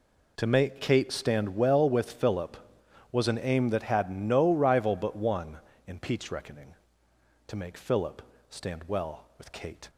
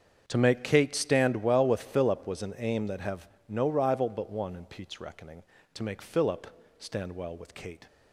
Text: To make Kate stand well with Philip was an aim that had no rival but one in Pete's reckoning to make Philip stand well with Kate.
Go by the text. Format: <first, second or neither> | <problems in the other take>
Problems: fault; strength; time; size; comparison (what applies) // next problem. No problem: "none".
first | starts louder than the rest; strong; until 1.2 s; 7.5 dB // says "have" for "had"; at 3.0 s // pauses between "Philip" and "stand"; slight; at 6.4 s; 0.30 s long; slight in the first